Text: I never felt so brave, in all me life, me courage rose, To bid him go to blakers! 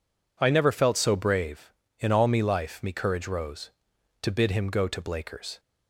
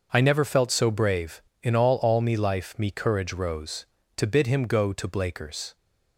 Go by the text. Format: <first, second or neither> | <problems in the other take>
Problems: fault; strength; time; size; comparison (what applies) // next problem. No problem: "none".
first | says "all" twice; at 1.9 s